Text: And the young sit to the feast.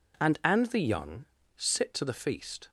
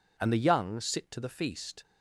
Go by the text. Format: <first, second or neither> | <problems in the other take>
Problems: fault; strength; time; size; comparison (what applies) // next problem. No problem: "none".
second | says "And" twice; at 0.4 s // pauses between "young" and "sit"; slight; at 1.2 s; 0.32 s long